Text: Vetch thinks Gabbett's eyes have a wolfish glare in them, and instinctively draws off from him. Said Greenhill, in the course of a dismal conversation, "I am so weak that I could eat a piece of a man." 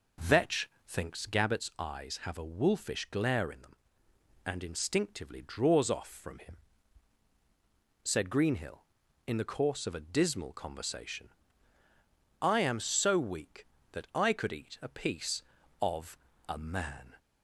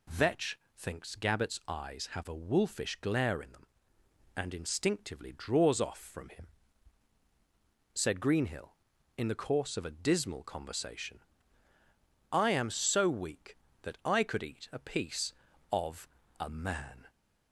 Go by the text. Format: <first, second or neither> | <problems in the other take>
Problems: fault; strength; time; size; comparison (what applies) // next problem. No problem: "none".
second | starts louder than the rest; noticeable; until 1.5 s; 5 dB // pauses between "Vetch" and "thinks"; slight; at 0.6 s; 0.18 s long; slight in the second // pauses between "of" and "a"; slight; at 16.1 s; 0.31 s long; slight in the second